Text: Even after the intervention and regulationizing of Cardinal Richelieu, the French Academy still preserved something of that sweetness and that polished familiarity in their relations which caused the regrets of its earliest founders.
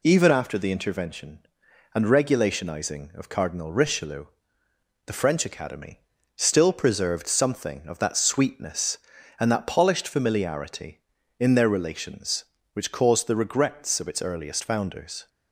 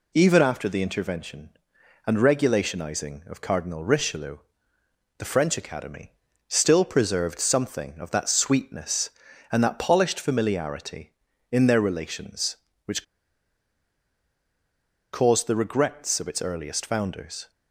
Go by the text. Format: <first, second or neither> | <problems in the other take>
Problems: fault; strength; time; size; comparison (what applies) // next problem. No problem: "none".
first | pauses between "Academy" and "still"; slight; at 6.1 s; 0.36 s long; slight in the first // pauses between "which" and "caused"; strong; at 13.0 s; 2.0 s long